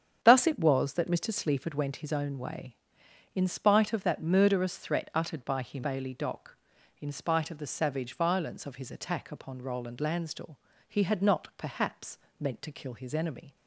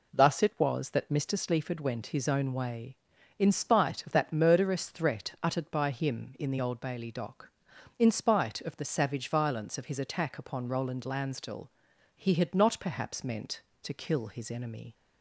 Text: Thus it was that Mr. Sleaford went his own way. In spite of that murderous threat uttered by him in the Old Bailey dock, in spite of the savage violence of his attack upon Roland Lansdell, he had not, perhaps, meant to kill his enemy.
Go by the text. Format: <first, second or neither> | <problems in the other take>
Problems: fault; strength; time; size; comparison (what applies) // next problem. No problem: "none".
second | starts louder than the rest; strong; until 1.2 s; 8 dB // skips "in the Old"; at 5.8 s